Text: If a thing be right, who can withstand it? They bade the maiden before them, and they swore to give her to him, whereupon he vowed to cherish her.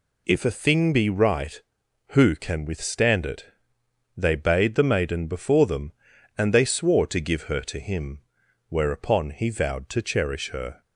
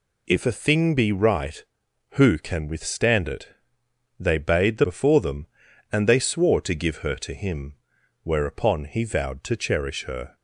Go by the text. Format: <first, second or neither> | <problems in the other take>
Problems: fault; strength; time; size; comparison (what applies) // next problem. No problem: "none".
first | skips "maiden"; at 4.8 s